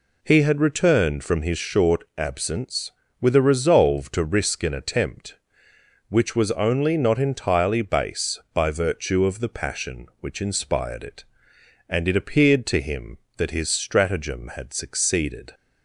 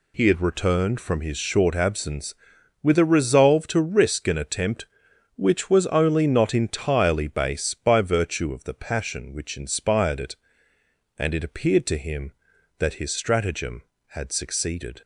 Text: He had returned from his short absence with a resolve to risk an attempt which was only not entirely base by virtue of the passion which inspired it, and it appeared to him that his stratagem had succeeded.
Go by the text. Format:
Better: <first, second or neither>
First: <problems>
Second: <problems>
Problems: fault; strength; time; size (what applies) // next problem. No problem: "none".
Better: neither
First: none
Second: none